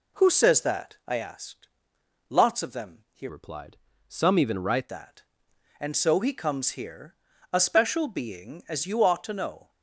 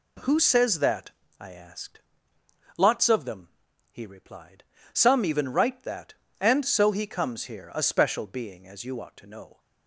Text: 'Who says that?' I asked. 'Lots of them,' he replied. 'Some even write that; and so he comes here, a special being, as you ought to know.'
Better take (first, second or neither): second